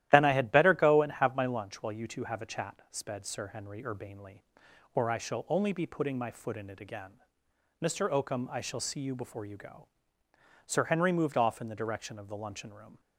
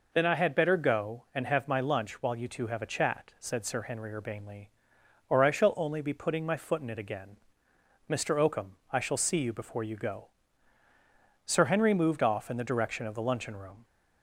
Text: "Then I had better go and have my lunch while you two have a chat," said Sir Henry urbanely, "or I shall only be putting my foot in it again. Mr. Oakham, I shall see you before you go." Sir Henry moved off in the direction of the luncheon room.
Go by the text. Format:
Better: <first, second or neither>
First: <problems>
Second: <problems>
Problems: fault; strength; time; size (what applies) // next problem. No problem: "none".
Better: second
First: starts louder than the rest; strong; until 1.1 s; 13 dB // says "sped" for "said"; at 2.9 s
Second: none